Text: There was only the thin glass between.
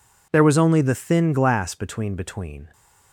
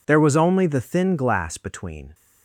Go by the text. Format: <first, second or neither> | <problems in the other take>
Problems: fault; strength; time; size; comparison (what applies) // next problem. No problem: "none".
second | says "between" twice; at 2.1 s